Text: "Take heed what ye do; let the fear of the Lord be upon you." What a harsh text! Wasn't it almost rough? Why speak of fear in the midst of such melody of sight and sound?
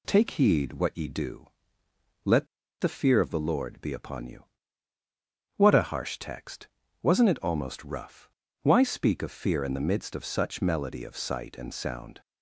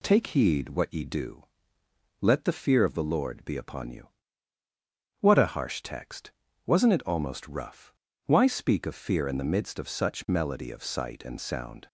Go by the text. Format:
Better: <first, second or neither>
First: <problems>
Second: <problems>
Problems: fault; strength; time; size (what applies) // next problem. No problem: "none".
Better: second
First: pauses between "let" and "the"; slight; at 2.4 s; 0.34 s long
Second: none